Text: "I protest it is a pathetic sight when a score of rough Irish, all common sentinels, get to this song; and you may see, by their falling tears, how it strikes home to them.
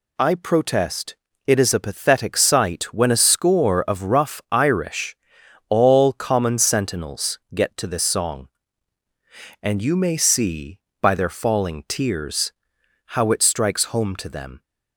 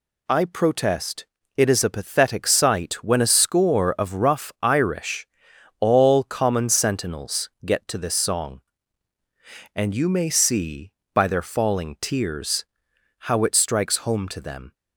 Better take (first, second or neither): neither